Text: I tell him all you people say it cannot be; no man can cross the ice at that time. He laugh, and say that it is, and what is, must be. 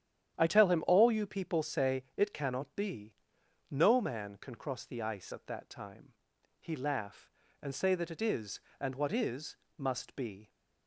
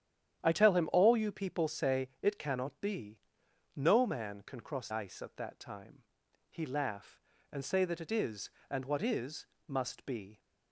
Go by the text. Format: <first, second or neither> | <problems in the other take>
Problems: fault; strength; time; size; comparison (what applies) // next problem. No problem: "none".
first | starts louder than the rest; strong; until 1.4 s; 10 dB; strong in the first // skips "the"; at 4.8 s